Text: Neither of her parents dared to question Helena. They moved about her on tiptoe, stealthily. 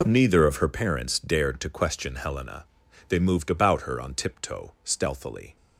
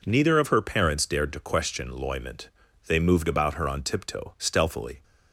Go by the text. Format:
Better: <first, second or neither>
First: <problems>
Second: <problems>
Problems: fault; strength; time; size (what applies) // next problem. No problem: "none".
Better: first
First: none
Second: says "Loyment" for "Helena"; at 1.8 s